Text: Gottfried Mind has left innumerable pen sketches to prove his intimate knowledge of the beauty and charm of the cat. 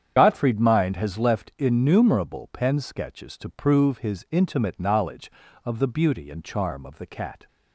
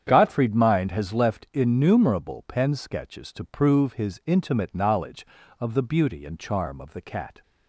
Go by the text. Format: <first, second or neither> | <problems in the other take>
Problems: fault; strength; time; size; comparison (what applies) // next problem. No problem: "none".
second | loses the start of "Gottfried"; at 0.1 s; 45 ms // starts louder than the rest; strong; until 1.1 s; 8.5 dB; strong in the second